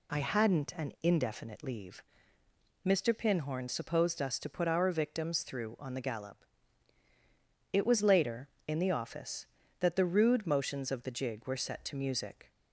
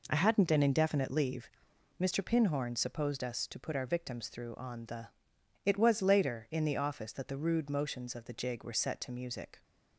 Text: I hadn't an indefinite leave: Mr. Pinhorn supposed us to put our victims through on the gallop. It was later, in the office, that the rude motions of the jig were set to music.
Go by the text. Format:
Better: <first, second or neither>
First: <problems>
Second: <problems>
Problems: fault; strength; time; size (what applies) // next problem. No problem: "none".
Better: first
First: none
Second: skips "gallop"; at 5.3 s